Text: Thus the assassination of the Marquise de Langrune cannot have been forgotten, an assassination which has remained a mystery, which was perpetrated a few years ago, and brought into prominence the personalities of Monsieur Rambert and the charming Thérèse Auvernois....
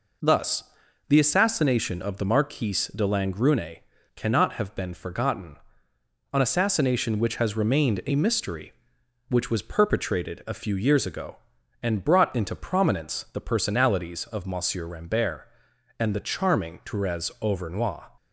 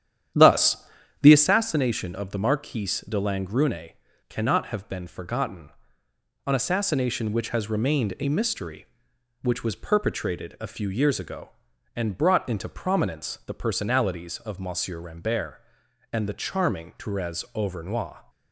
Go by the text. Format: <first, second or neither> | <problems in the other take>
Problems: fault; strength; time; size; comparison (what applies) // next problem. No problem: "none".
first | starts louder than the rest; strong; until 1.6 s; 10 dB // pauses between "Thus" and "the"; at 0.7 s; 0.44 s long; also in the first // pauses between "Langrune" and "cannot"; slight; at 3.9 s; 0.34 s long; slight in the first